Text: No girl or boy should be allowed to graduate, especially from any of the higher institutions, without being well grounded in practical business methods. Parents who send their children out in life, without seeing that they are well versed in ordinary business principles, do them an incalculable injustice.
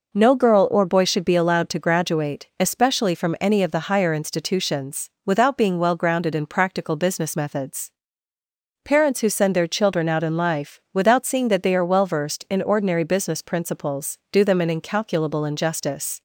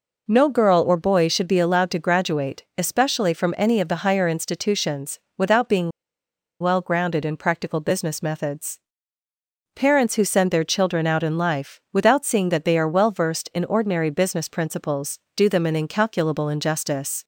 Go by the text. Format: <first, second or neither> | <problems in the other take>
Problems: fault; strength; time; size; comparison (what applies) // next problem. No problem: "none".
first | pauses between "being" and "well"; noticeable; at 5.9 s; 0.70 s long